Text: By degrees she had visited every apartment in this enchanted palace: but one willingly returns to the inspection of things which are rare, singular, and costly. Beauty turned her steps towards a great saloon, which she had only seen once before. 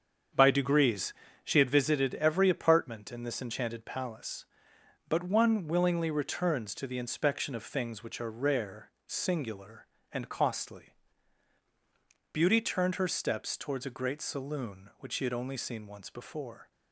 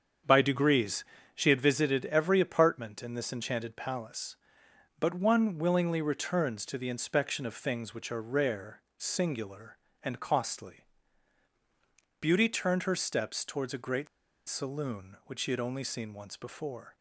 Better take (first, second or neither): first